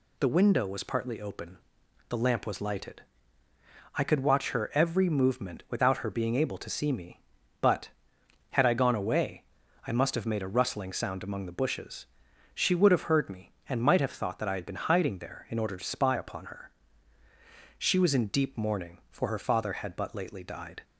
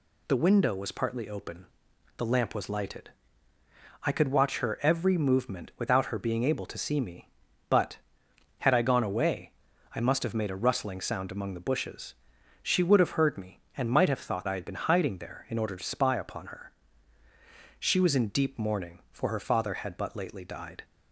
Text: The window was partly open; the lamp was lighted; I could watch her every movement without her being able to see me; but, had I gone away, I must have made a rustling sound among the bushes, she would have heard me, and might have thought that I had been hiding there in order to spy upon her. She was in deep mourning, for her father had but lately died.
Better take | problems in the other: first | skips "that"; at 14.4 s

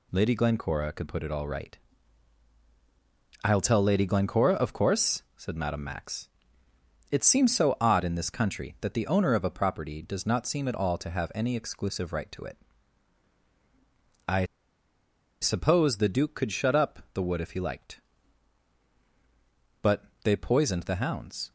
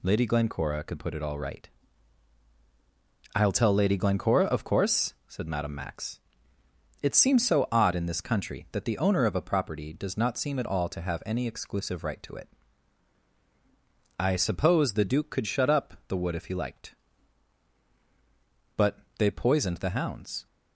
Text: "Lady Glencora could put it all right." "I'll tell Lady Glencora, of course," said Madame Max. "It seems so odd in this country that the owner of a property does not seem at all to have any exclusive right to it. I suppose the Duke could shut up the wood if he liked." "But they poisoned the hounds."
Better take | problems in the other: second | pauses between "I" and "suppose"; noticeable; at 14.4 s; 0.96 s long // pauses between "But" and "they"; slight; at 20.0 s; 0.20 s long; slight in the second

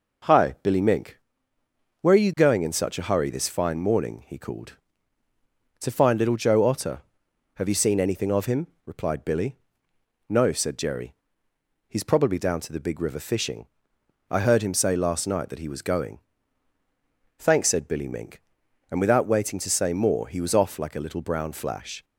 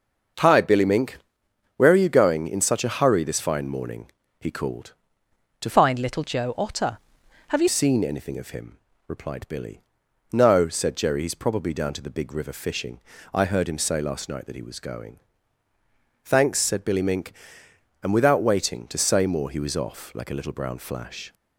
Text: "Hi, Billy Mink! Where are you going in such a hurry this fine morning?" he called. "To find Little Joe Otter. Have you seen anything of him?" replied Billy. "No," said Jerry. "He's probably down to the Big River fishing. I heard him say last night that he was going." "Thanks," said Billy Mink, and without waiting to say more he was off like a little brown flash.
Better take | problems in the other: first | starts louder than the rest; until 2.0 s; 6.5 dB // changes voice from "find" to "you"; from 5.6 to 7.6 s; 2.0 s long

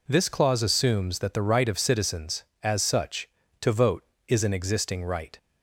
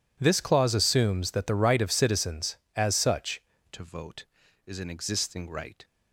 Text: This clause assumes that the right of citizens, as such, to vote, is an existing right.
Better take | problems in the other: first | changes voice at "to"; from 3.7 s on; 2.1 s long

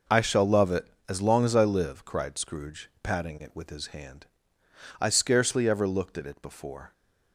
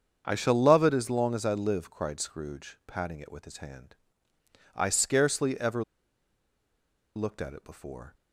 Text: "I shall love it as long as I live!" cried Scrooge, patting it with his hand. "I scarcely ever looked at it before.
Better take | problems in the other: first | starts louder than the rest; strong; until 1.2 s; 7.5 dB // pauses between "ever" and "looked"; strong; at 5.8 s; 1.3 s long

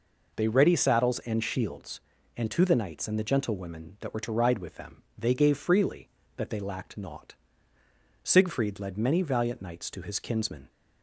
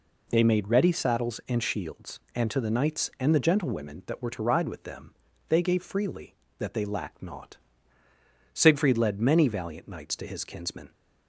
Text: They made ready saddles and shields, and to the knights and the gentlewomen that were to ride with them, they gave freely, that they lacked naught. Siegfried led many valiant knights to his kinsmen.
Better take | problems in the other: second | skips "made"; at 0.4 s

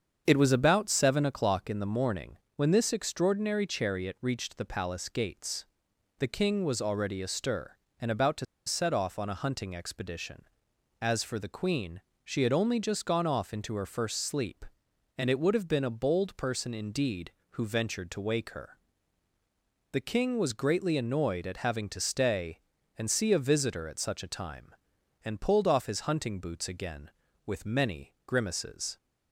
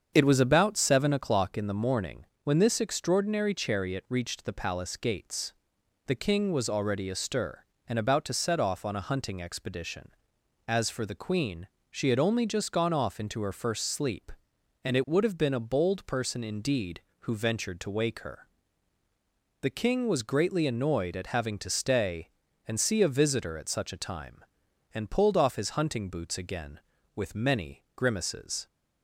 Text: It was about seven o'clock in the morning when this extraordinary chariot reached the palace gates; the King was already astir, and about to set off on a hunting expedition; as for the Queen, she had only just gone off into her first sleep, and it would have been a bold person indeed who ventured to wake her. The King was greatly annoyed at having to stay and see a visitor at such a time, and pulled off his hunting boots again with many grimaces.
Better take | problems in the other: second | starts louder than the rest; strong; until 1.2 s; 7 dB; strong in the second // pauses between "morning" and "when"; slight; at 2.3 s; 0.18 s long; slight in the second // pauses between "to" and "set"; slight; at 8.4 s; 0.21 s long

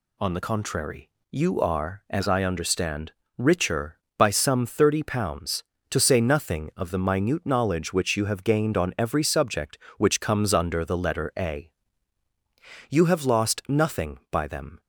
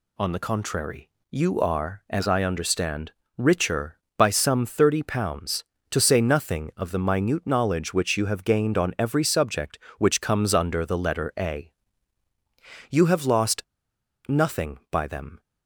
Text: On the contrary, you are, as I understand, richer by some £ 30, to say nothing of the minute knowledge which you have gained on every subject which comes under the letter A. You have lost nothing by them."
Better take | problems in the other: first | pauses between "lost" and "nothing"; noticeable; at 13.6 s; 0.65 s long

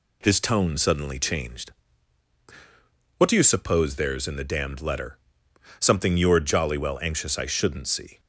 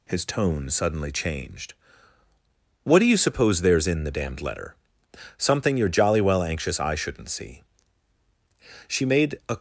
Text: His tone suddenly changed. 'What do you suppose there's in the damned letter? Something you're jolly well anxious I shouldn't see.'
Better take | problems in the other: first | goes on to say "She made a"; noticeable; from 8.8 s on; 0.70 s long

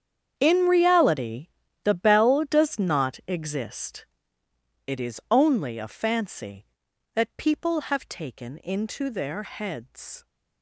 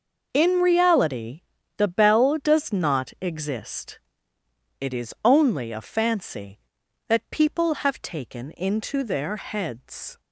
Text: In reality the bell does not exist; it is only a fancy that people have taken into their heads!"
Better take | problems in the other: second | gets quieter; strong; throughout; 17 dB // pauses between "reality" and "the"; at 1.4 s; 0.38 s long; also in the second

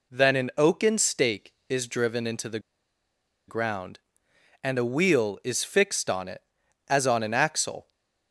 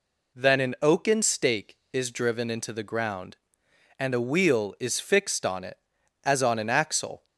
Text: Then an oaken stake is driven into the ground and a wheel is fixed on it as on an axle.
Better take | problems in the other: second | pauses between "the" and "ground"; noticeable; at 2.5 s; 0.89 s long

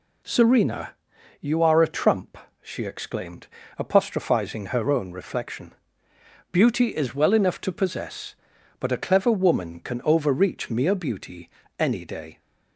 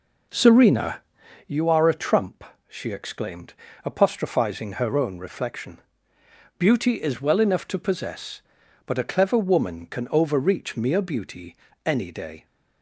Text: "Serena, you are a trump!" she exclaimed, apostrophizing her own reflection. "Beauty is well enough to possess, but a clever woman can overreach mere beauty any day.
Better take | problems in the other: first | starts louder than the rest; noticeable; until 1.5 s; 4.5 dB // pauses between "beauty" and "any"; slight; at 11.5 s; 0.28 s long; slight in the first

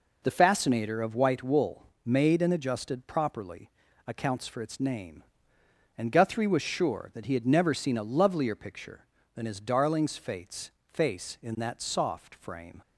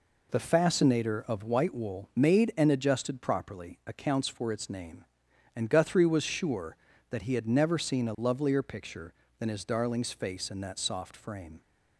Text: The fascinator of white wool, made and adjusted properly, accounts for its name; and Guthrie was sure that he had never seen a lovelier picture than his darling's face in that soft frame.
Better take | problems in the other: second | says "face" twice; at 10.8 s

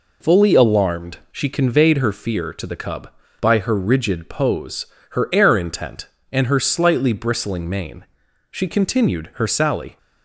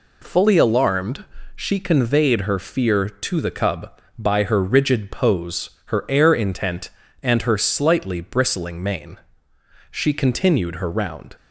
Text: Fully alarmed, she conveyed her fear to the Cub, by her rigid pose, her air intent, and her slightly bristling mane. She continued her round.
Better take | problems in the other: second | says "sally" for "round"; at 9.4 s

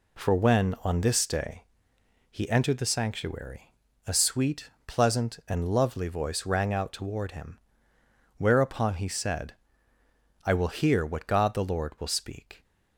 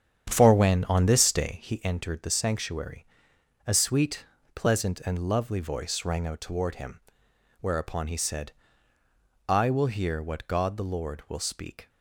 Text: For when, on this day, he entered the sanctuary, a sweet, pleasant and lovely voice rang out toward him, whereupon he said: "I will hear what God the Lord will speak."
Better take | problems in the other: first | starts louder than the rest; strong; until 1.9 s; 8.5 dB

